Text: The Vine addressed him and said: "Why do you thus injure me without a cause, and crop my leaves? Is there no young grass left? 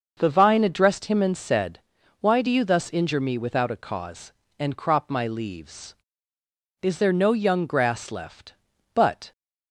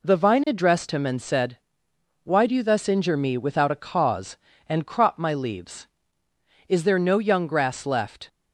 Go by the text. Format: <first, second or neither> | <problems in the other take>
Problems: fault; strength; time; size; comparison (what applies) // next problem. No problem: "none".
second | starts louder than the rest; noticeable; until 1.1 s; 6 dB // goes on to say "But"; slight; from 8.9 s on; 0.38 s long